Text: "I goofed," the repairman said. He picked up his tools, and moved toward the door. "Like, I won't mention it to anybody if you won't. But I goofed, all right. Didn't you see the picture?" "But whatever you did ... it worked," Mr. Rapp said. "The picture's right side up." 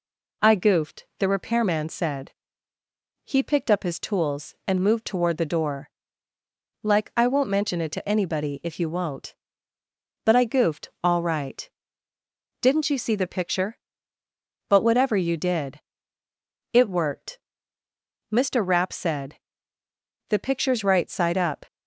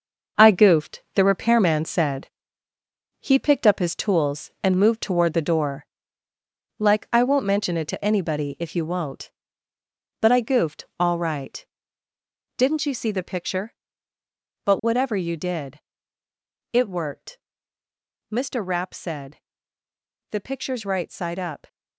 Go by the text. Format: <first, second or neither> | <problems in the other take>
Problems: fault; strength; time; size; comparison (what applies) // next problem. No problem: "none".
first | gets quieter; strong; throughout; 8.5 dB